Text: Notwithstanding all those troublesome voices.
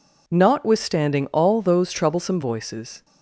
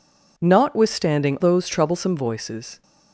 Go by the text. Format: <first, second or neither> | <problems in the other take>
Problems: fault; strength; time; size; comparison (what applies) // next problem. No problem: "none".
first | skips "all"; at 1.3 s